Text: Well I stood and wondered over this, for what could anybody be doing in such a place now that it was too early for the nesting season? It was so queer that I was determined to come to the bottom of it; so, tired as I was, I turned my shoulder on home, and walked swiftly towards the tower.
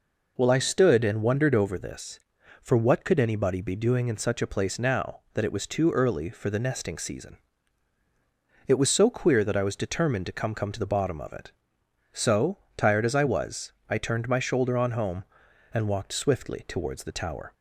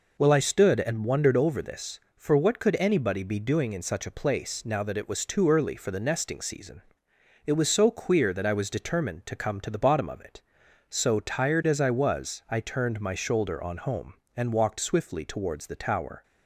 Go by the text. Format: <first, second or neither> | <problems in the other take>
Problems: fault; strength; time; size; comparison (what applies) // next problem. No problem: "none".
second | says "come" twice; at 10.5 s